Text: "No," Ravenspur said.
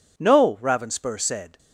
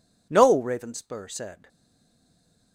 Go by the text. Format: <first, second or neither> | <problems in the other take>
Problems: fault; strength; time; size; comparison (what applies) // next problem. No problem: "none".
first | stays silent after the last word; from 1.6 s on; 1.1 s long